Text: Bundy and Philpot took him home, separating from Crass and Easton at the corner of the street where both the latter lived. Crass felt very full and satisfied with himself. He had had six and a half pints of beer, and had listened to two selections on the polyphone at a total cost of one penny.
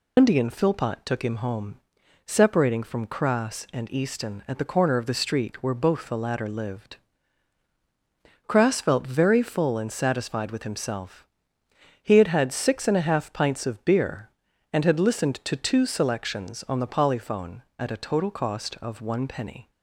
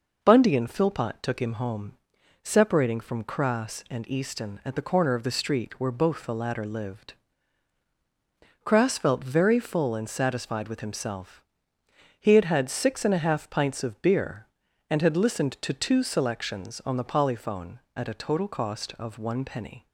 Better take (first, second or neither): second